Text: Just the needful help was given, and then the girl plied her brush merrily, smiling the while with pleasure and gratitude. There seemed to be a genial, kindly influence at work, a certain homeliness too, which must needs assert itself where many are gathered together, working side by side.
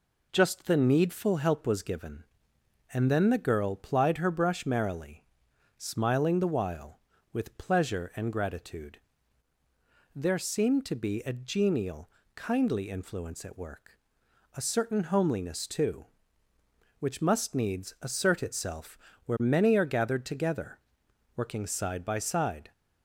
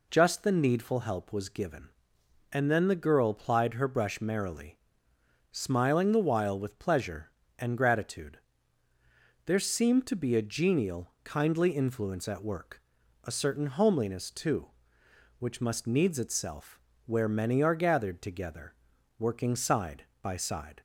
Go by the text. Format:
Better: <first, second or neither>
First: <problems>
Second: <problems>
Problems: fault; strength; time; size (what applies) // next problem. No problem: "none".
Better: first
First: pauses between "itself" and "where"; slight; at 18.9 s; 0.26 s long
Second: skips "assert"; at 16.1 s // pauses between "itself" and "where"; slight; at 16.7 s; 0.26 s long